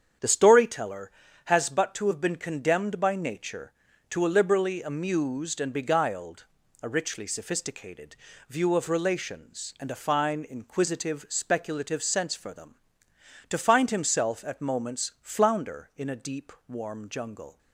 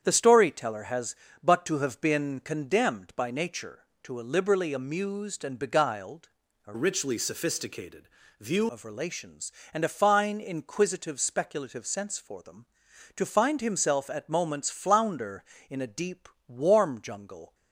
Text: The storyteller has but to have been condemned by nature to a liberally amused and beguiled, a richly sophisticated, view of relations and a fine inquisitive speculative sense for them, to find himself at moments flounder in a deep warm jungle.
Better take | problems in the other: first | starts louder than the rest; strong; until 1.0 s; 8 dB; strong in the first // changes voice from "richly" to "view"; from 6.7 to 8.6 s; 1.9 s long // pauses between "deep" and "warm"; slight; at 16.2 s; 0.18 s long; slight in the first

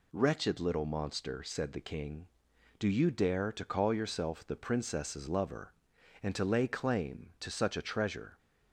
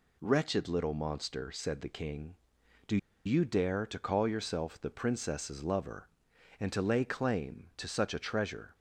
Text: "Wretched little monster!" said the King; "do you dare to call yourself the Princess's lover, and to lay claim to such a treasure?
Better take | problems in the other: first | pauses between "do" and "you"; slight; at 2.9 s; 0.28 s long

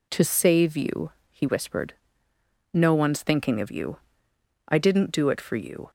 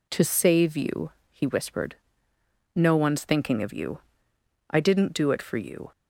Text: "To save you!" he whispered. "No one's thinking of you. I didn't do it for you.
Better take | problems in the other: neither | none

